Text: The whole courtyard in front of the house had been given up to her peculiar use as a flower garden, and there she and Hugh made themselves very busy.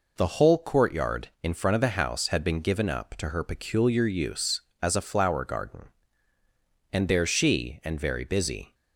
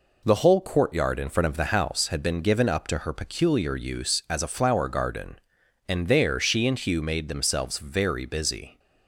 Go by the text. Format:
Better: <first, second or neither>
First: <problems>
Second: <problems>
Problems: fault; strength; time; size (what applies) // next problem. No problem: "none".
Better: second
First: skips "Hugh made themselves"; at 7.9 s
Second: none